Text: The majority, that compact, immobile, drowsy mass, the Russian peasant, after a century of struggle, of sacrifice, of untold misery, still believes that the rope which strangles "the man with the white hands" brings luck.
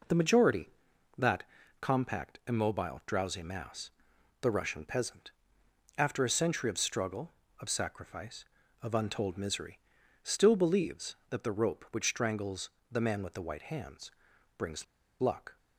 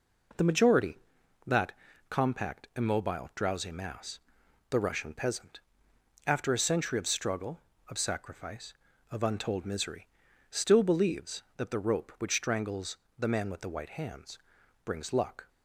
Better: second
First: pauses between "that" and "compact"; slight; at 1.4 s; 0.36 s long // pauses between "strangles" and "the"; slight; at 12.6 s; 0.22 s long // pauses between "hands" and "brings"; noticeable; at 14.1 s; 0.46 s long // pauses between "brings" and "luck"; slight; at 14.8 s; 0.35 s long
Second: pauses between "that" and "compact"; slight; at 1.7 s; 0.36 s long // pauses between "strangles" and "the"; slight; at 12.9 s; 0.22 s long // pauses between "hands" and "brings"; noticeable; at 14.3 s; 0.46 s long

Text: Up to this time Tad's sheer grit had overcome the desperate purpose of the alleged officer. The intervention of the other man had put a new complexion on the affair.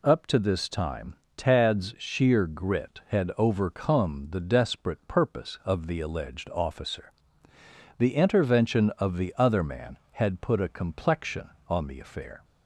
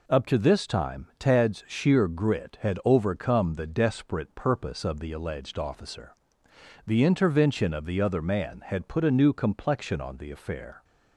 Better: second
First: pauses between "time" and "Tad's"; slight; at 1.1 s; 0.20 s long // skips "new"; at 10.7 s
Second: none

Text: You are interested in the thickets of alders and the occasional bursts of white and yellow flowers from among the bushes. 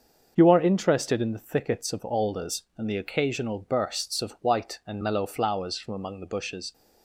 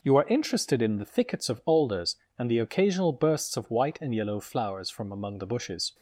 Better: second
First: starts louder than the rest; until 1.3 s; 6.5 dB // says "mellow" for "yellow"; at 5.0 s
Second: none

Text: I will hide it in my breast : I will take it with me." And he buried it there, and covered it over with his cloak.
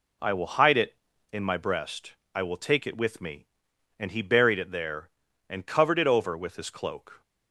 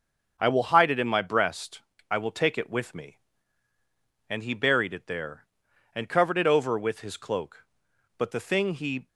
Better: first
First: none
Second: starts louder than the rest; until 1.4 s; 6.5 dB // goes on to say "But the thing he"; noticeable; from 8.1 s on; 0.90 s long

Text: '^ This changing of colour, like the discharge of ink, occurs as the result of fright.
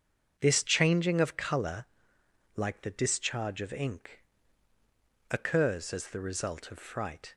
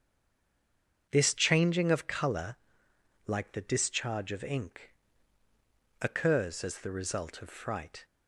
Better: first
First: starts louder than the rest; until 1.3 s; 7 dB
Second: stays silent before the first word; until 1.0 s; 1.0 s long // starts louder than the rest; until 2.0 s; 7 dB

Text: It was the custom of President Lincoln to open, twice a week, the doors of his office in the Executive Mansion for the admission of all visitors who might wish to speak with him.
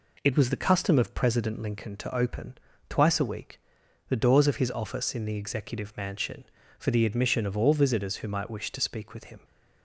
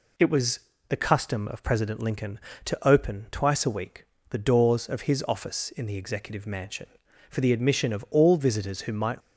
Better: first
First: none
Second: pauses between "was" and "the"; slight; at 0.6 s; 0.28 s long // stops before "wish to speak with him"; at 9.2 s

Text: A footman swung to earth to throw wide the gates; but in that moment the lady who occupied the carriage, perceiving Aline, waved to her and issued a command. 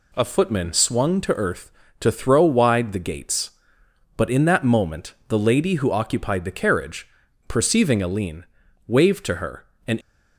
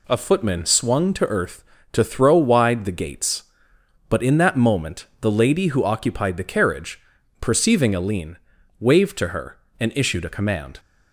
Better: second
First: stops before "issued a command"; at 10.0 s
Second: none

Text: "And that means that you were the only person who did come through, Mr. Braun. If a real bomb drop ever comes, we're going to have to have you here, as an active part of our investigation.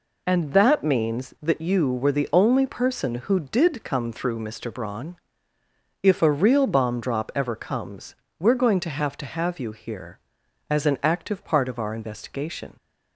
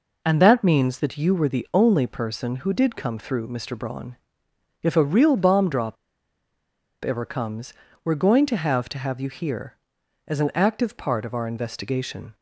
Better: first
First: none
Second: pauses between "drop" and "ever"; at 5.9 s; 1.0 s long

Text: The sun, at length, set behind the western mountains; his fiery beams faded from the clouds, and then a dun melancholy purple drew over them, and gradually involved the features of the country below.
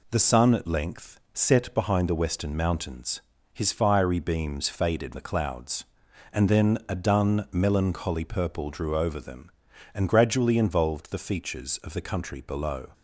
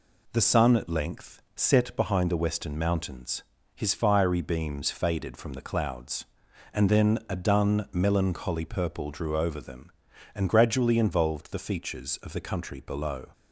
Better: second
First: skips "from"; at 5.1 s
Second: none

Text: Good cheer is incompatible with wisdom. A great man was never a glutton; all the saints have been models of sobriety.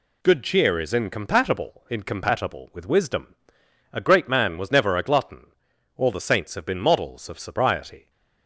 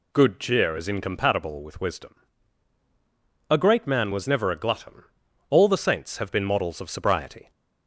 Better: second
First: says "incompatible" twice; at 1.8 s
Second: none

